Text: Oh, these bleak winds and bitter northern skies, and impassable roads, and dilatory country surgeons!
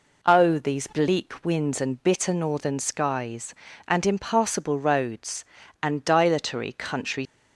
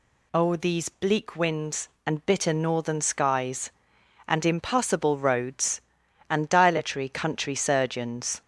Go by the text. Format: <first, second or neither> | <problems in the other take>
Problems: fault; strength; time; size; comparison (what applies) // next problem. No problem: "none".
second | stops before "surgeons"; at 7.2 s